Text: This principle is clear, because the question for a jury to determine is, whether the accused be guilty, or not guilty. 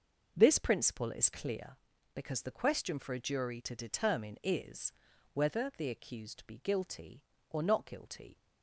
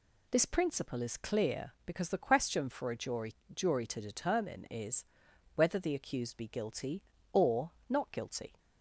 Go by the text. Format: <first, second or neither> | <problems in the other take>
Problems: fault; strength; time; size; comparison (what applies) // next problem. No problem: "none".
first | says "jury" twice; at 3.5 s // pauses between "or" and "not"; slight; at 7.7 s; 0.16 s long